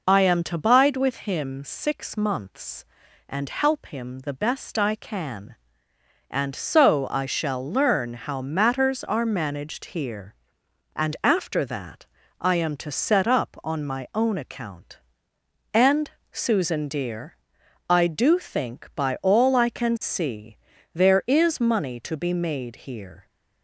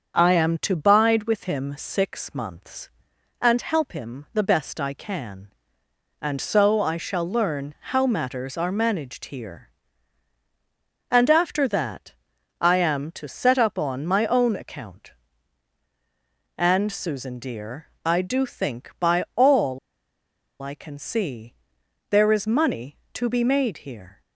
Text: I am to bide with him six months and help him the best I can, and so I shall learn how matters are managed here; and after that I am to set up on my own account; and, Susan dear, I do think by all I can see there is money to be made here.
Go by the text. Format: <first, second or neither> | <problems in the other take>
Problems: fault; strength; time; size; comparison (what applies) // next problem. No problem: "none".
first | starts louder than the rest; until 1.1 s; 7 dB // pauses between "learn" and "how"; slight; at 7.7 s; 0.18 s long // pauses between "that" and "I"; noticeable; at 12.1 s; 0.48 s long; slight in the first // pauses between "all" and "I"; noticeable; at 19.7 s; 0.83 s long // pauses between "see" and "there"; noticeable; at 21.5 s; 0.56 s long; also in the first